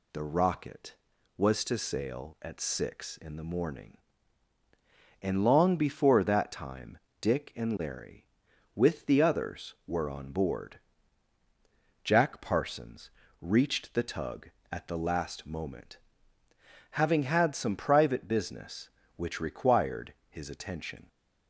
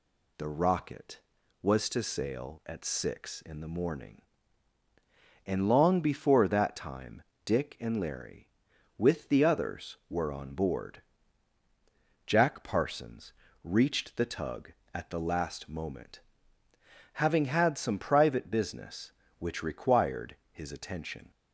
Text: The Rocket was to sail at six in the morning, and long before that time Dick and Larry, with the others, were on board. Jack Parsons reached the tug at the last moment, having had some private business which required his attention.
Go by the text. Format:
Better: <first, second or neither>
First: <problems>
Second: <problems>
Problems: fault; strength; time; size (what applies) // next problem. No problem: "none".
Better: neither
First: pauses between "time" and "Dick"; slight; at 6.9 s; 0.22 s long // pauses between "Parsons" and "reached"; slight; at 13.0 s; 0.30 s long // pauses between "required" and "his"; slight; at 20.1 s; 0.16 s long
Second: pauses between "time" and "Dick"; slight; at 7.2 s; 0.22 s long // pauses between "Parsons" and "reached"; slight; at 13.3 s; 0.30 s long // pauses between "required" and "his"; slight; at 20.3 s; 0.16 s long